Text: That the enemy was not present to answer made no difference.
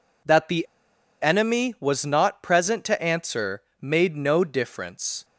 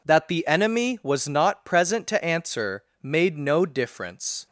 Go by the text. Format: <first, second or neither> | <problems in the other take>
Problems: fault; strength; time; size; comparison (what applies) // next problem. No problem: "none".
second | pauses between "the" and "enemy"; noticeable; at 0.6 s; 0.57 s long // pauses between "answer" and "made"; slight; at 3.6 s; 0.18 s long; slight in the second